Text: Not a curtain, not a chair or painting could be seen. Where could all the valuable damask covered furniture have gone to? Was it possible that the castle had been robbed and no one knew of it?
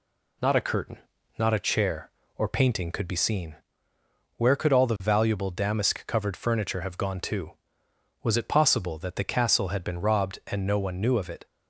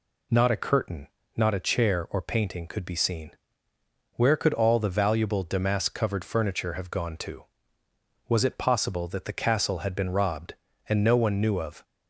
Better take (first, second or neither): first